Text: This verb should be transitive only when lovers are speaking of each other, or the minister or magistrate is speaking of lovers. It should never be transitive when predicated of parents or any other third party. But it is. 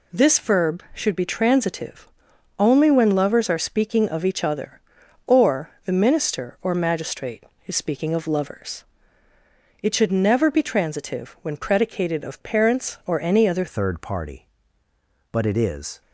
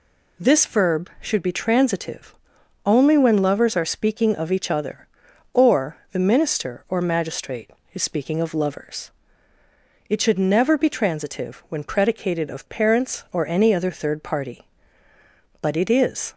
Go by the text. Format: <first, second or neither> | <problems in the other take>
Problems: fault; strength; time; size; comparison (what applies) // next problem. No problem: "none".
second | pauses between "transitive" and "only"; noticeable; at 2.0 s; 0.50 s long; noticeable in the second // changes voice at "third"; from 13.6 s on; 2.4 s long